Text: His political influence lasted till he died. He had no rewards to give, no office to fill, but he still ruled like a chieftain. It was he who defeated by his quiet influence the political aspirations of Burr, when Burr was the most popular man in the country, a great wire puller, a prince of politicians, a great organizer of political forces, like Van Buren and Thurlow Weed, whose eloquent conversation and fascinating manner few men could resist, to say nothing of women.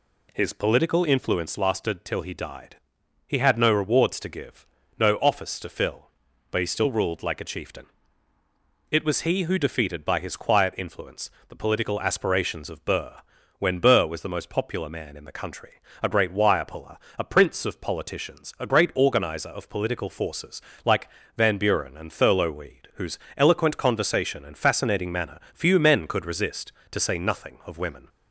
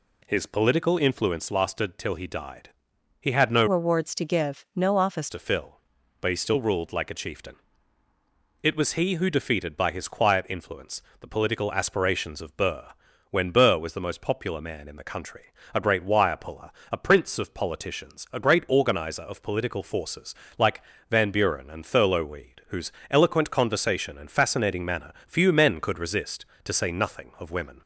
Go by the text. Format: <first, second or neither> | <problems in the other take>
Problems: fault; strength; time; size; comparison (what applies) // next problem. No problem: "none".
first | changes voice from "rewards" to "office"; from 3.6 to 5.2 s; 1.6 s long // pauses between "influence" and "the"; slight; at 11.0 s; 0.20 s long; slight in the first // pauses between "like" and "Van"; slight; at 20.8 s; 0.28 s long; slight in the first // pauses between "whose" and "eloquent"; slight; at 22.9 s; 0.18 s long; slight in the first // pauses between "manner" and "few"; slight; at 25.1 s; 0.16 s long; slight in the first